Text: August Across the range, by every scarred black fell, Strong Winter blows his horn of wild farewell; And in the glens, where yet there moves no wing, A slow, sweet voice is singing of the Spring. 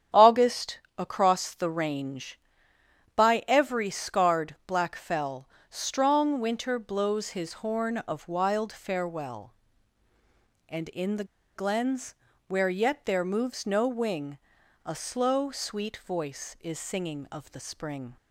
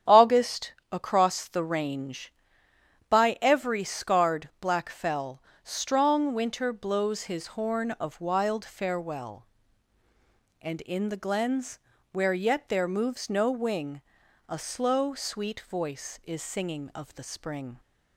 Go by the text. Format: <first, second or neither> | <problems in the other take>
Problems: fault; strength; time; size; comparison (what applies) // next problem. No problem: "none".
second | starts louder than the rest; strong; until 1.3 s; 9 dB; strong in the second // pauses between "August" and "Across"; slight; at 0.7 s; 0.20 s long; slight in the second // pauses between "the" and "glens"; slight; at 11.2 s; 0.31 s long